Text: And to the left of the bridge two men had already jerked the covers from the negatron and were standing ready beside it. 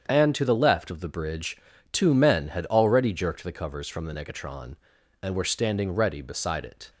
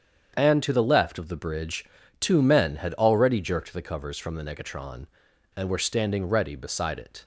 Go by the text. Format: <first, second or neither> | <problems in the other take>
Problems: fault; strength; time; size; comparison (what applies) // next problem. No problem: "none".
neither | starts louder than the rest; strong; the same in both // pauses between "bridge" and "two"; slight; the same in both